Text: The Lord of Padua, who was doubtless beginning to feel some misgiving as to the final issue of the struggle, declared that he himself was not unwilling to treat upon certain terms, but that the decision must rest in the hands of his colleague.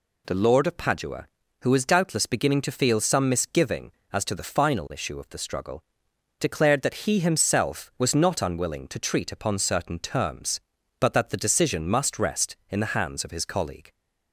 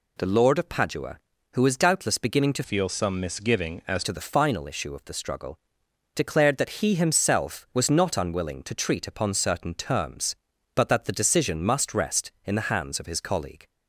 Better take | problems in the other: first | changes voice from "feel" to "as"; from 2.6 to 4.0 s; 1.4 s long

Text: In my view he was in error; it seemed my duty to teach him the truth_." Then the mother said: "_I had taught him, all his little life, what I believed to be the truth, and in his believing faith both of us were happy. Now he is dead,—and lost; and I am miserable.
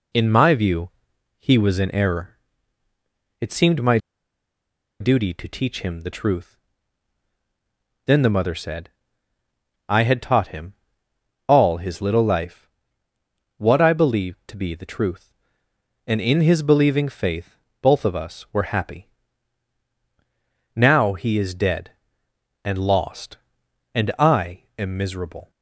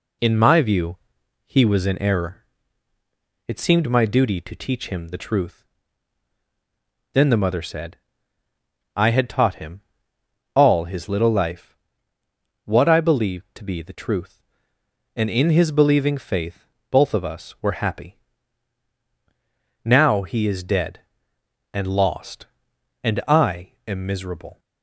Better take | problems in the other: second | pauses between "view" and "he"; noticeable; at 0.8 s; 0.48 s long; noticeable in the second // pauses between "my" and "duty"; at 3.9 s; 1.0 s long // pauses between "faith" and "both"; slight; at 17.5 s; 0.24 s long; slight in the second

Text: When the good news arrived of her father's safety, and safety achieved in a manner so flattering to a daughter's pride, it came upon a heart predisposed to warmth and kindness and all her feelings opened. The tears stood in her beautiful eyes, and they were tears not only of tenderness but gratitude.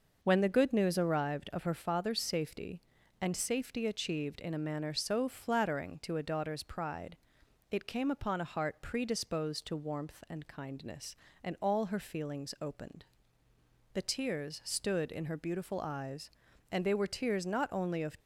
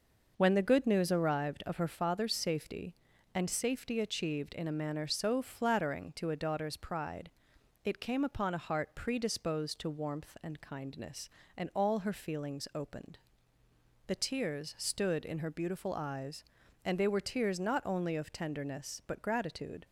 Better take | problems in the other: second | stops before "tenderness but gratitude"; at 18.1 s

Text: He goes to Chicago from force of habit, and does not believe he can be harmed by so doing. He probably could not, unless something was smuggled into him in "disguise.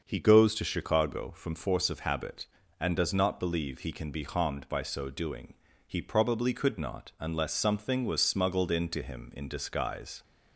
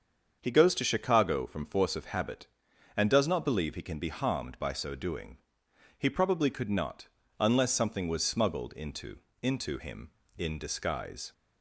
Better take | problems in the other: first | starts louder than the rest; until 1.4 s; 7 dB; also in the first // says "into" twice; at 9.4 s

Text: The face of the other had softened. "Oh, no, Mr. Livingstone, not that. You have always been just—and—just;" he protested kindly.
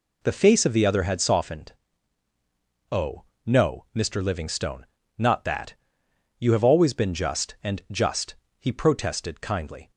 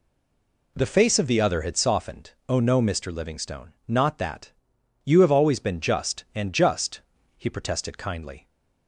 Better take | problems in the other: first | stays silent before the first word; slight; until 0.7 s; 0.7 s long

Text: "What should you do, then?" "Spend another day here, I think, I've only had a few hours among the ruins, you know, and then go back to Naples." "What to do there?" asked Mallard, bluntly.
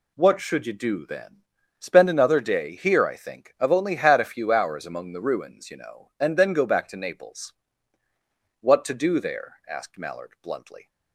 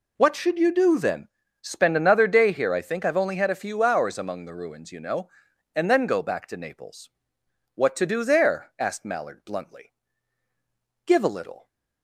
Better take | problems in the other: first | goes on to say "Give a little"; noticeable; from 11.0 s on; 0.64 s long

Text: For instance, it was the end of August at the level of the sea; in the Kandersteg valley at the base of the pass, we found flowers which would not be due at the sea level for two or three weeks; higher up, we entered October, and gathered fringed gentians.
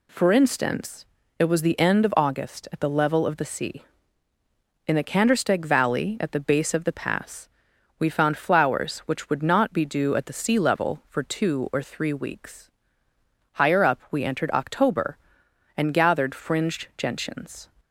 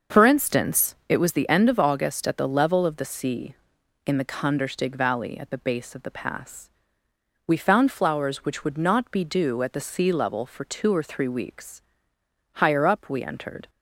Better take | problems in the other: first | starts louder than the rest; noticeable; until 1.2 s; 6 dB // stops before "October and gathered fringed gentians"; at 13.6 s

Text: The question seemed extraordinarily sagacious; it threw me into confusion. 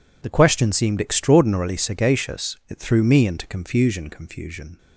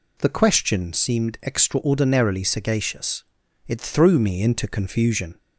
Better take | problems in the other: second | says "confusion" twice; at 4.0 s

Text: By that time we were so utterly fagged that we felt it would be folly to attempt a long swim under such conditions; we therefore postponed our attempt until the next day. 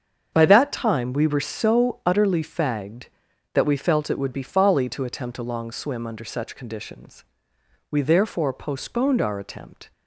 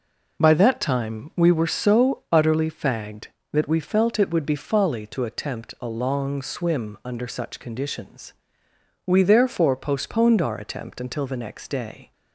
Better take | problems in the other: second | starts louder than the rest; strong; until 1.3 s; 7 dB // stops before "until the next day"; at 9.9 s

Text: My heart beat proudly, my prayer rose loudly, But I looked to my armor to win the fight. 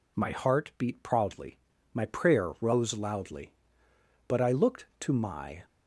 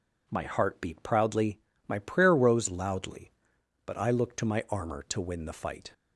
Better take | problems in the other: second | stops before "armor to win the fight"; at 5.6 s

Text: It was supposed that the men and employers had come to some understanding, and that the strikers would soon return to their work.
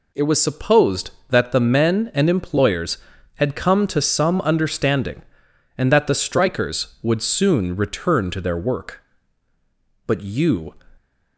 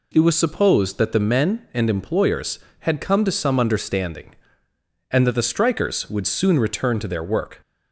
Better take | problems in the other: second | goes on to say "But you"; noticeable; from 10.0 s on; 0.66 s long

